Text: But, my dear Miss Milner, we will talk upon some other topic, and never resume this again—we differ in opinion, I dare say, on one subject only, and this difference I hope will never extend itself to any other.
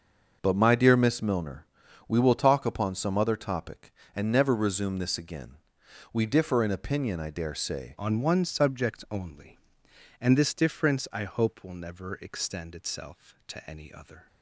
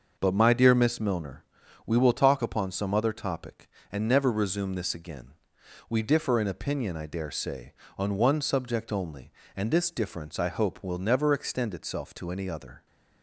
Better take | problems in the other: second | starts louder than the rest; until 1.4 s; 6.5 dB; noticeable in the second // changes voice at "on"; from 7.9 s on; 6.3 s long

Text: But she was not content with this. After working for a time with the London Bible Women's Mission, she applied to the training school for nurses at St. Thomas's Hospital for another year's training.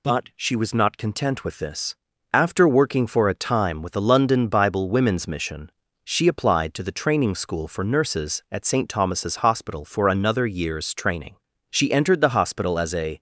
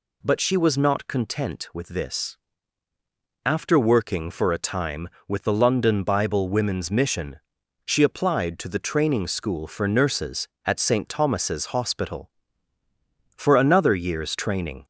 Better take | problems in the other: second | goes on to say "She entered the hospital as a"; from 11.7 s on; 1.4 s long

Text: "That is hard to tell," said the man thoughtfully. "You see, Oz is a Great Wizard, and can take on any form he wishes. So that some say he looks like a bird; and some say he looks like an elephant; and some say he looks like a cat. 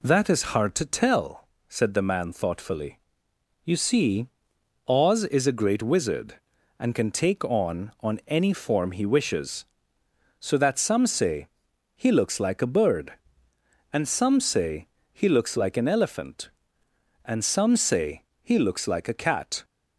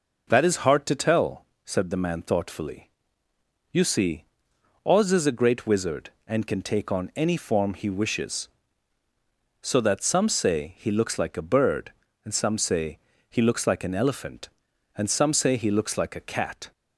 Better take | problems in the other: second | says "on" twice; at 8.0 s // pauses between "say" and "he"; noticeable; at 11.4 s; 0.46 s long // pauses between "say" and "he"; slight; at 14.8 s; 0.24 s long; slight in the second // pauses between "say" and "he"; slight; at 18.2 s; 0.18 s long

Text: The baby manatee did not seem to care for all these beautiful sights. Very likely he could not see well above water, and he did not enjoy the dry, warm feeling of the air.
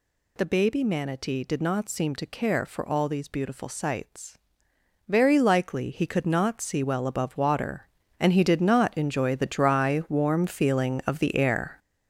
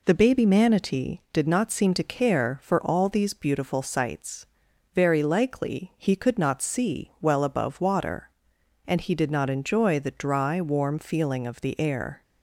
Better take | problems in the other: second | gets louder; strong; throughout; 7.5 dB

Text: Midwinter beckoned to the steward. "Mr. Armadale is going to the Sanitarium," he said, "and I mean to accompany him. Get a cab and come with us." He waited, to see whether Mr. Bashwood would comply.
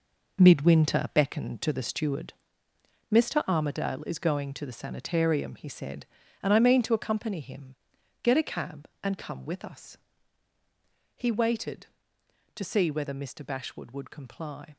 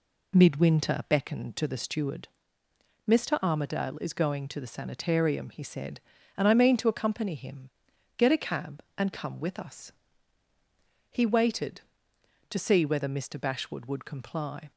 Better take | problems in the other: second | gets quieter; strong; throughout; 10 dB

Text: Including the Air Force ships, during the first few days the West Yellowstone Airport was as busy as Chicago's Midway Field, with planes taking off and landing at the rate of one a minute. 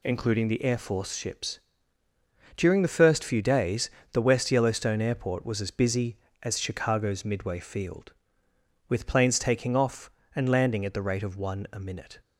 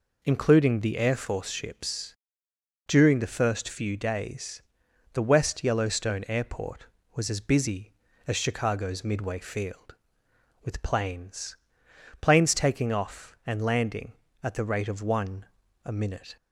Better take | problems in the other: first | pauses between "days" and "the"; noticeable; at 4.6 s; 0.52 s long; slight in the first // says "planes" twice; at 12.1 s // pauses between "one" and "a"; at 15.4 s; 0.38 s long

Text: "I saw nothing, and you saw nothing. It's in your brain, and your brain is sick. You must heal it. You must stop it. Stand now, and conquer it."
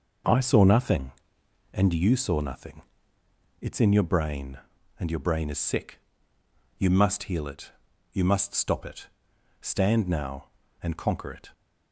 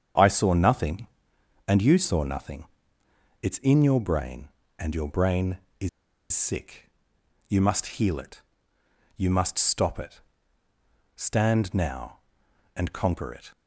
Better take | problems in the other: first | starts louder than the rest; strong; until 1.7 s; 7.5 dB // pauses between "is" and "sick"; at 5.8 s; 0.43 s long

